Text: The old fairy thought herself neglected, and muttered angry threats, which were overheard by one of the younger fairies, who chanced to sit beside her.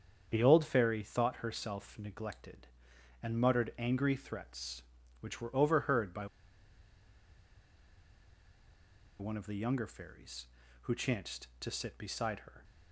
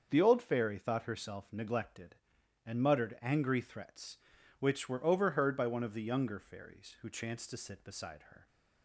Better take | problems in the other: second | starts louder than the rest; strong; until 1.3 s; 7.5 dB; also in the second // pauses between "by" and "one"; strong; at 6.2 s; 2.9 s long

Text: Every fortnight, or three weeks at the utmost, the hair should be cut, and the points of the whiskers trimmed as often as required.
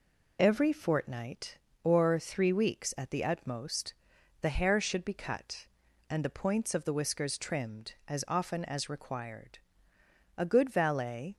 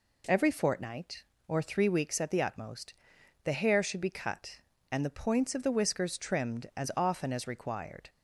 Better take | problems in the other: second | goes on to say "A good valet"; noticeable; from 10.3 s on; 0.98 s long

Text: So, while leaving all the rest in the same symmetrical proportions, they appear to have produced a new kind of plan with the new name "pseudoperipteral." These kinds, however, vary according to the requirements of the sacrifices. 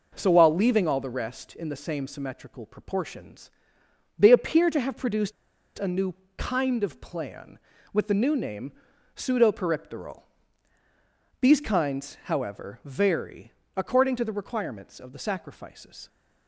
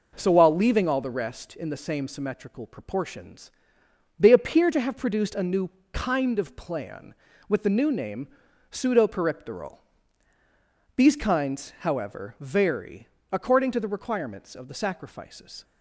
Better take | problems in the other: second | pauses between "produced" and "a"; at 5.3 s; 0.45 s long // pauses between "new" and "kind"; slight; at 6.1 s; 0.24 s long; slight in the second // pauses between "name" and "pseudoperipteral"; at 8.7 s; 0.44 s long; also in the second // pauses between "vary" and "according"; slight; at 13.5 s; 0.24 s long; slight in the second

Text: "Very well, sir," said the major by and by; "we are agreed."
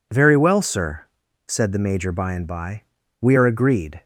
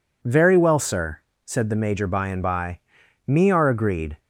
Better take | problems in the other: first | says "me" for "we"; at 3.2 s

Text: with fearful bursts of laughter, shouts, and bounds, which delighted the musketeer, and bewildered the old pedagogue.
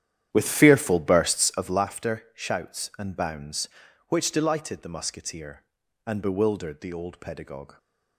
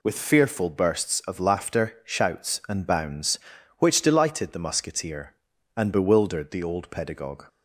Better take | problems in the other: second | starts louder than the rest; strong; until 1.9 s; 10.5 dB

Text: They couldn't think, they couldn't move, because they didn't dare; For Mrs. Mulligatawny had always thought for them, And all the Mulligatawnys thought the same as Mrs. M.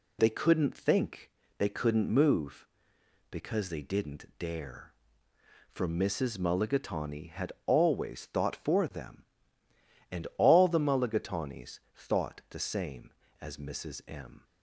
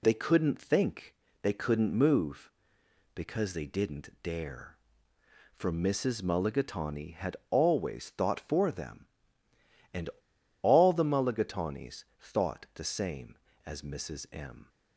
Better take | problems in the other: first | pauses between "And" and "all"; noticeable; at 10.0 s; 0.53 s long // pauses between "Mulligatawnys" and "thought"; slight; at 12.0 s; 0.16 s long; slight in the first

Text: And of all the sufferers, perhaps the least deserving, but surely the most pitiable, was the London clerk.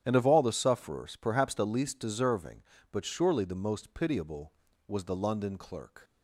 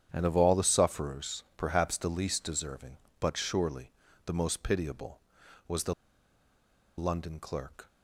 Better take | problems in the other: first | starts louder than the rest; strong; until 1.1 s; 9 dB; strong in the first // pauses between "surely" and "the"; slight; at 3.9 s; 0.32 s long // pauses between "the" and "London"; at 5.9 s; 1.0 s long

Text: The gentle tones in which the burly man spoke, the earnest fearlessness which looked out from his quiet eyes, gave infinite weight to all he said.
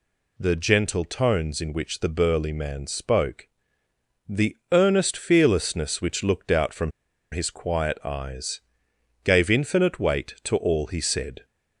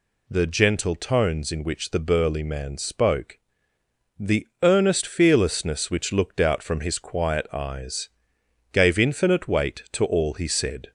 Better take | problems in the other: second | pauses between "the" and "earnest"; slight; at 4.5 s; 0.16 s long; slight in the second // pauses between "from" and "his"; at 6.9 s; 0.41 s long

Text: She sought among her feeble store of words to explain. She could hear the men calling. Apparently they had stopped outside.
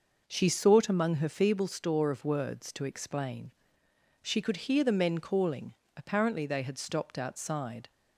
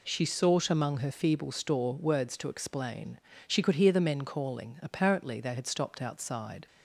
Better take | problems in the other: first | skips "of"; at 1.9 s

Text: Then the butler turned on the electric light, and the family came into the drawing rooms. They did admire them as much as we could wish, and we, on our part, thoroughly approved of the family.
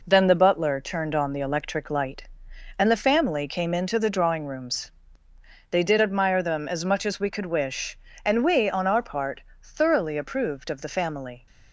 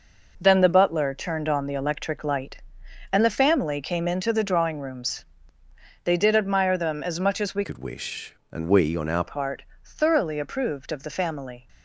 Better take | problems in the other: first | changes voice from "could" to "our"; from 7.6 to 9.2 s; 1.6 s long

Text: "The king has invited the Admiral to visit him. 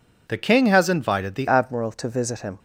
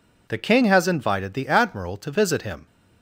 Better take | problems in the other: second | changes voice at "Admiral"; from 1.4 s on; 1.1 s long

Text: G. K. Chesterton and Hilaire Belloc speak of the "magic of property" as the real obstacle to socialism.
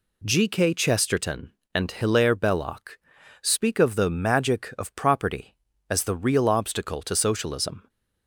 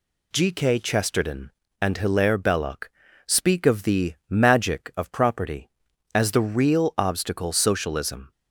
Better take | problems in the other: first | pauses between "Belloc" and "speak"; at 2.8 s; 0.38 s long; also in the first // skips "to"; at 7.5 s

